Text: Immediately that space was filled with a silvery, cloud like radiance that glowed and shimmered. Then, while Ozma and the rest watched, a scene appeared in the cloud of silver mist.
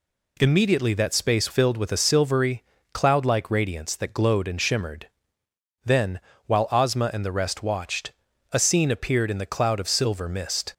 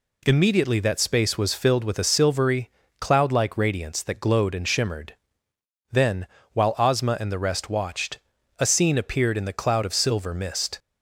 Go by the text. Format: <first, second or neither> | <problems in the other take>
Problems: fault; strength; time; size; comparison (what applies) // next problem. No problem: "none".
second | skips "was"; at 1.4 s